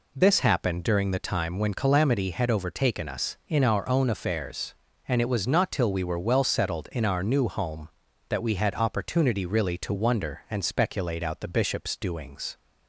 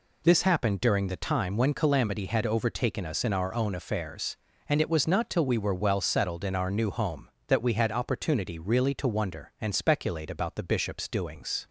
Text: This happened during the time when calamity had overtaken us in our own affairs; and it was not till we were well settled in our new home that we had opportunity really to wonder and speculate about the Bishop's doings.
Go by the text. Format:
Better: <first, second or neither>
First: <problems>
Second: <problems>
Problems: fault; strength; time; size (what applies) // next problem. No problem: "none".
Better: second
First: says "out" for "about"; at 11.2 s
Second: none